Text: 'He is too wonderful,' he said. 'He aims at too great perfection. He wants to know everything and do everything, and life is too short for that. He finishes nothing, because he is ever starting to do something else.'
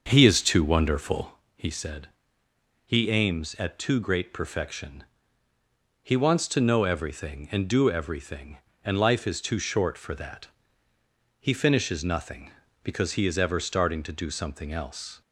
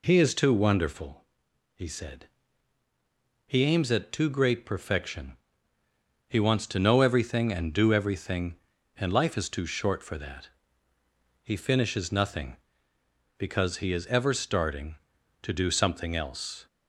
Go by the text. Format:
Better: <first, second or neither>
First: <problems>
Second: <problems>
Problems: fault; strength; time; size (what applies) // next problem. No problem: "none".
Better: second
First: starts louder than the rest; until 1.3 s; 6.5 dB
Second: none